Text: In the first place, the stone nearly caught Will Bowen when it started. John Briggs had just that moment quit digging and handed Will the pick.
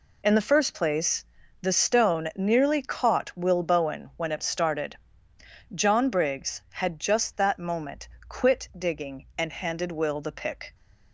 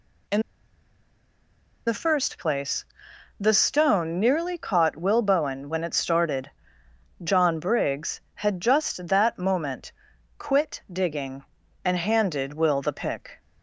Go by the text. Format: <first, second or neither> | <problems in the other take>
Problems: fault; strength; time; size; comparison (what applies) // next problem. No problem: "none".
first | pauses between "In" and "the"; strong; at 0.4 s; 1.4 s long // pauses between "moment" and "quit"; noticeable; at 9.9 s; 0.46 s long; slight in the first